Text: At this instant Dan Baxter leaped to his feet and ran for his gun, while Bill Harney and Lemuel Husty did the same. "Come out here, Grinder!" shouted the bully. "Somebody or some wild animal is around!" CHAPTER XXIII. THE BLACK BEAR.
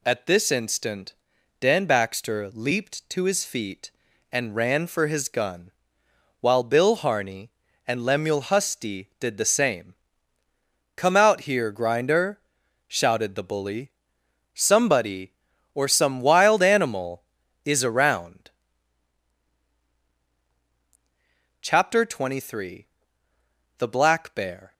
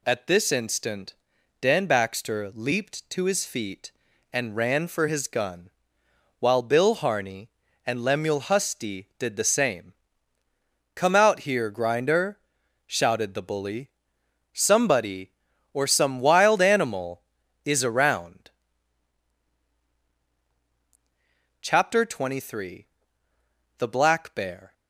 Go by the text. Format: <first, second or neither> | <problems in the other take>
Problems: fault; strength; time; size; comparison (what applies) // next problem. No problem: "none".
neither | pauses between "instant" and "Dan"; noticeable; the same in both